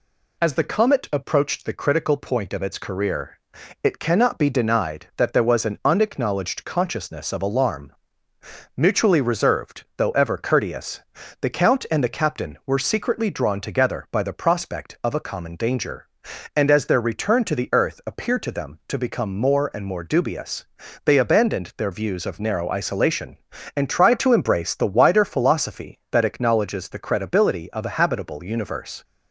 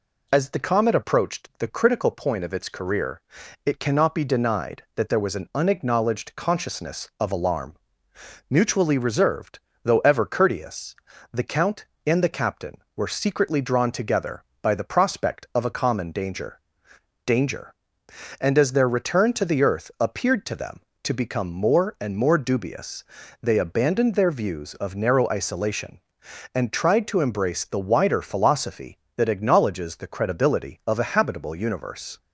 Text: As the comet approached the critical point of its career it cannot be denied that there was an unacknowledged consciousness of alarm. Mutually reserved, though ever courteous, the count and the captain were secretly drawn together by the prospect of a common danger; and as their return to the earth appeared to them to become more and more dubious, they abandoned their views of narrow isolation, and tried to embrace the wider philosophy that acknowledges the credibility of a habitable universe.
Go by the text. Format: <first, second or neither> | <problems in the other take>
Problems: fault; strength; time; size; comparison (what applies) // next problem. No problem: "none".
first | pauses between "career" and "it"; at 3.2 s; 0.42 s long; also in the first // says "danger" twice; at 17.2 s